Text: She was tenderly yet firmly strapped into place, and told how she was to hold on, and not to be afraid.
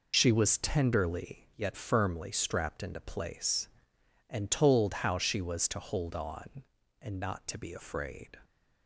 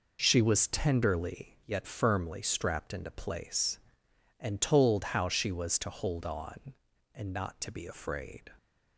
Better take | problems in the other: second | loses the start of "She"; at 0.1 s; 40 ms

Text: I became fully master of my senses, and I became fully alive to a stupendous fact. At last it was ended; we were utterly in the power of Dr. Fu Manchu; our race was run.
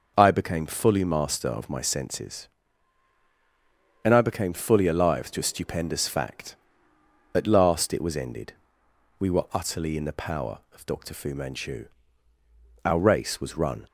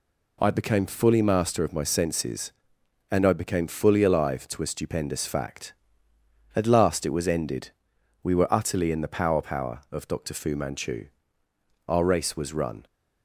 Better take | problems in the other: first | says "power" twice; at 9.4 s

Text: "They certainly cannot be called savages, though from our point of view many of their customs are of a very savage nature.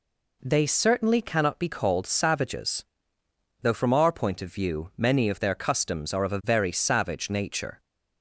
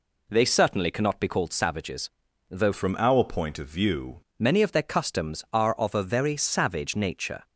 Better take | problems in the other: first | changes voice from "from" to "view"; from 2.7 to 4.2 s; 1.5 s long

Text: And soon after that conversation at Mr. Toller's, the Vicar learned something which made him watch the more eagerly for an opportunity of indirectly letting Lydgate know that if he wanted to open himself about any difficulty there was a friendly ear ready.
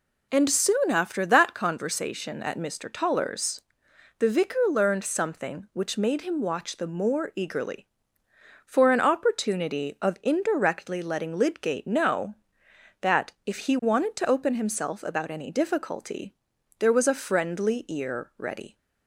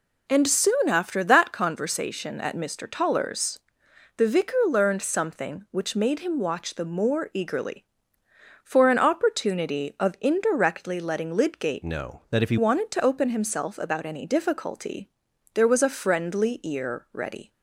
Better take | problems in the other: first | changes voice from "know" to "he"; from 11.8 to 12.5 s; 0.7 s long // pauses between "difficulty" and "there"; noticeable; at 15.0 s; 0.46 s long; noticeable in the first

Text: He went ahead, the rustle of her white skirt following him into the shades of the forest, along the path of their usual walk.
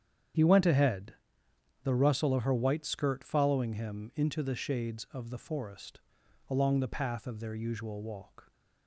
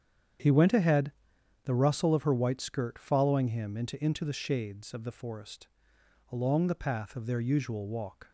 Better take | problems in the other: first | starts louder than the rest; strong; until 1.9 s; 8.5 dB; strong in the first // says "into" twice; at 4.0 s

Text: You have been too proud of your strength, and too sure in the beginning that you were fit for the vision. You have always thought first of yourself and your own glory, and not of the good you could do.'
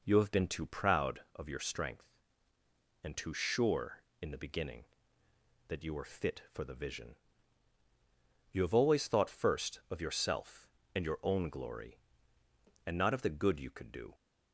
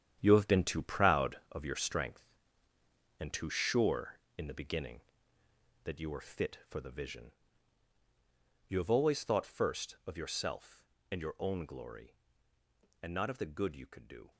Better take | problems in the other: first | gets quieter; strong; throughout; 11 dB

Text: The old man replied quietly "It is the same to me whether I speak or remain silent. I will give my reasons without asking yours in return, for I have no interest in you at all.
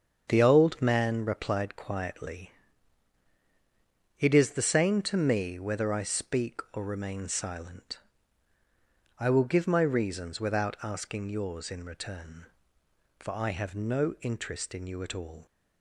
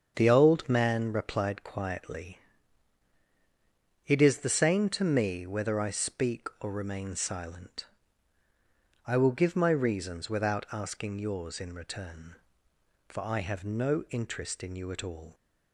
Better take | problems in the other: neither | starts louder than the rest; strong; the same in both // pauses between "quietly" and "It"; strong; the same in both

